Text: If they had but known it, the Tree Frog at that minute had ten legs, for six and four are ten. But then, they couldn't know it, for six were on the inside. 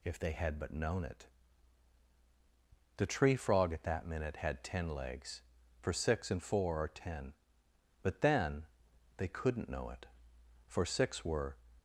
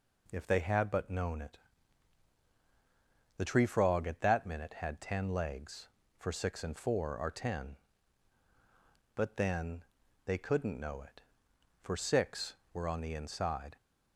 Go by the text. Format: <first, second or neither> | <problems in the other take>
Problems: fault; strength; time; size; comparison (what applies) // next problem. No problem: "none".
second | stops before "on the inside"; at 11.7 s